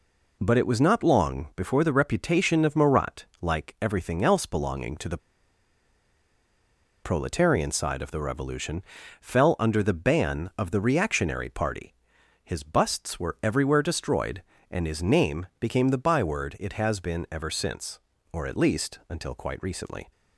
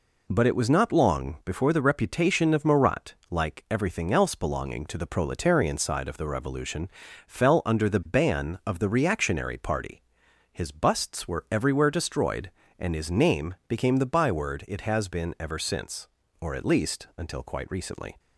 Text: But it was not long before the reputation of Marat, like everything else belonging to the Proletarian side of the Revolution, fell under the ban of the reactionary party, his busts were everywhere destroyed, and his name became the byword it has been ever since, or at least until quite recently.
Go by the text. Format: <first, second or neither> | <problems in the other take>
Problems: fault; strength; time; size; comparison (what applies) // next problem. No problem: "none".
second | pauses between "the" and "Proletarian"; strong; at 5.1 s; 1.8 s long